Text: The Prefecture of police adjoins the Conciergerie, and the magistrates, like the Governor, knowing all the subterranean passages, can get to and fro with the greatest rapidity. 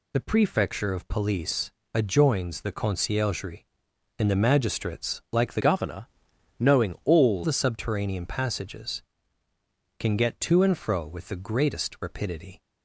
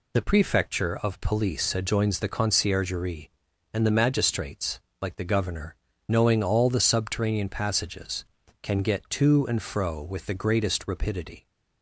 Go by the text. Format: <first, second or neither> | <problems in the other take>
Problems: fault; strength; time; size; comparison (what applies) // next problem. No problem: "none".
second | pauses between "police" and "adjoins"; slight; at 1.7 s; 0.22 s long // changes voice from "Governor" to "all"; from 5.6 to 7.4 s; 1.8 s long